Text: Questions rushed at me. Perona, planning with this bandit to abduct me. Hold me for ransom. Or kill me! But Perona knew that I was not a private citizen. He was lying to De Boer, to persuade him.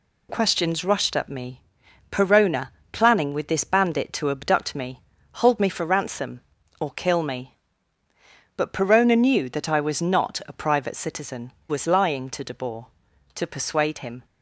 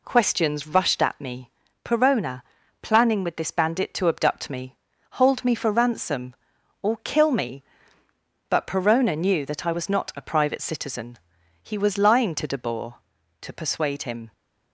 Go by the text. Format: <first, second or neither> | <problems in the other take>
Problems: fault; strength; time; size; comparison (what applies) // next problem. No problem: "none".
second | skips "He"; at 11.5 s